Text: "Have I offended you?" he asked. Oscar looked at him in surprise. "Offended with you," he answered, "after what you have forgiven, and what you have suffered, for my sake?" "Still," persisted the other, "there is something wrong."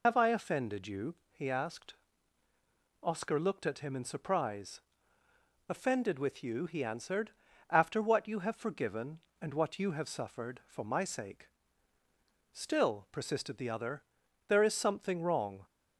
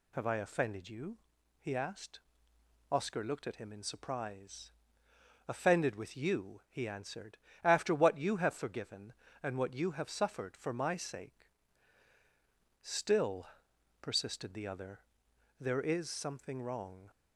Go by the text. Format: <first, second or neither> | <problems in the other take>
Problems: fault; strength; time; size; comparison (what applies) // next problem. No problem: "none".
second | loses the start of "Have"; at 0.0 s; 70 ms